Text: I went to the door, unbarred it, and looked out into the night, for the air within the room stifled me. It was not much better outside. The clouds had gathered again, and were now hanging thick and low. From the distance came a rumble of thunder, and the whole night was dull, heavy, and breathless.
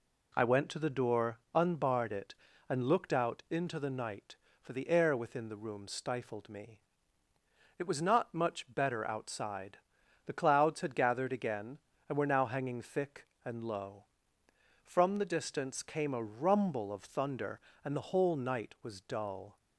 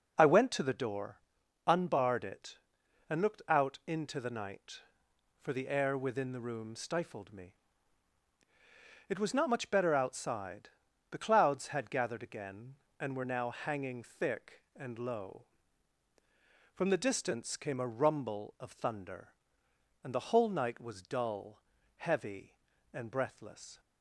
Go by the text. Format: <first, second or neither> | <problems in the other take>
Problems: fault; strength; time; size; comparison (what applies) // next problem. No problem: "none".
second | stops before "heavy and breathless"; at 19.5 s